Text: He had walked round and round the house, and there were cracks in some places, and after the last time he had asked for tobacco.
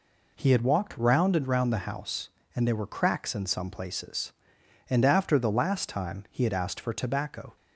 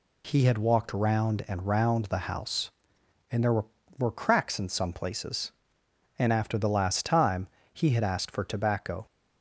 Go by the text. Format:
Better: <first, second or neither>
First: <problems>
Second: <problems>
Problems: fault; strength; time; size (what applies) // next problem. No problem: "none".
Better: first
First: none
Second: says "were" twice; at 3.9 s // pauses between "time" and "he"; slight; at 7.4 s; 0.26 s long